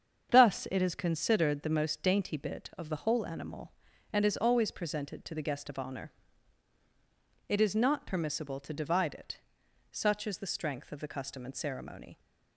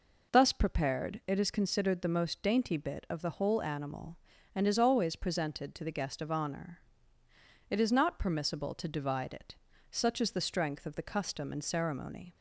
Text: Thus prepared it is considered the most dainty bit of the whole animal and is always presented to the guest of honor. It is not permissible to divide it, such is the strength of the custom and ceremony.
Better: second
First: starts louder than the rest; strong; until 1.3 s; 7.5 dB // skips "prepared"; at 0.6 s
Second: none

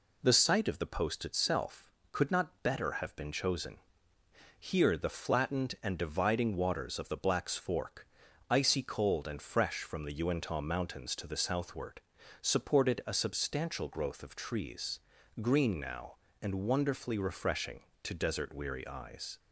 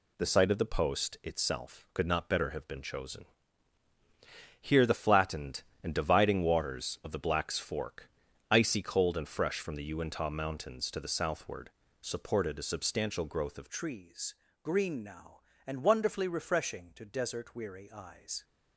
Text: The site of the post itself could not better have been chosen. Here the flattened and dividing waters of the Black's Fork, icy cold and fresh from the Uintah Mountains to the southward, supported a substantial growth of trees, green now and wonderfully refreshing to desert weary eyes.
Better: first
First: none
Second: changes voice at "trees"; from 13.6 s on; 4.8 s long

